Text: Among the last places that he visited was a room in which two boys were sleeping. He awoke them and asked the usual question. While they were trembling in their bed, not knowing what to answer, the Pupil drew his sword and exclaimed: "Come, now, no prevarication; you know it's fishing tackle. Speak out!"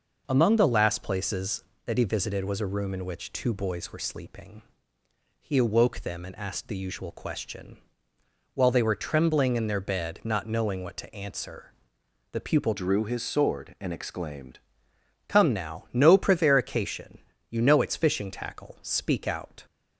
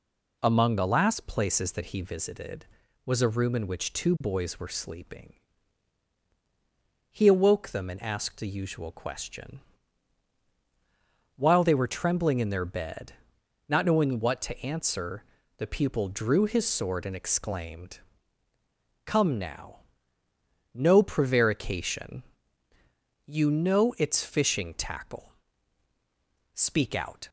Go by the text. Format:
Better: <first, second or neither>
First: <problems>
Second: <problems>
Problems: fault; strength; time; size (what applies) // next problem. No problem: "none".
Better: second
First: changes voice from "drew" to "exclaimed"; from 12.7 to 14.5 s; 1.8 s long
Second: none